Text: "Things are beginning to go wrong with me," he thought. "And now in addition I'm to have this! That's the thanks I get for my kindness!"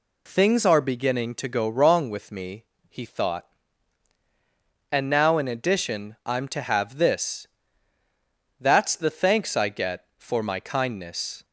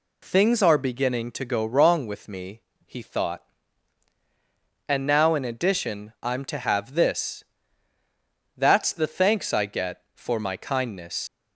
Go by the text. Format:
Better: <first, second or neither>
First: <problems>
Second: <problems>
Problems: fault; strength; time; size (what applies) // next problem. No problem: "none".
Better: first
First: none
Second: leaves "kindness" unfinished; at 11.2 s; 140 ms